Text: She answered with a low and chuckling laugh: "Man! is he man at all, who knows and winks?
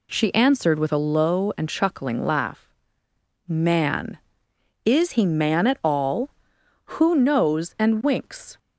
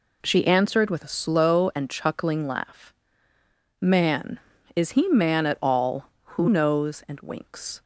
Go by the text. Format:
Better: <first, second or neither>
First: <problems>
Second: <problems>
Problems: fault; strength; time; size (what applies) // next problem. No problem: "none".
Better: first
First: none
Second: says "slow" for "low"; at 1.1 s